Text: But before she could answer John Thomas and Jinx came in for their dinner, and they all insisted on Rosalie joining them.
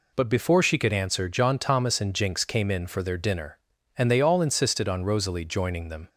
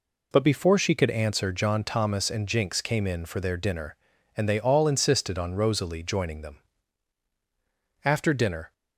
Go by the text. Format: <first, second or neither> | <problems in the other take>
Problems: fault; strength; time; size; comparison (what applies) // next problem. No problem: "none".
first | goes on to say "After dinner"; noticeable; from 8.0 s on; 0.68 s long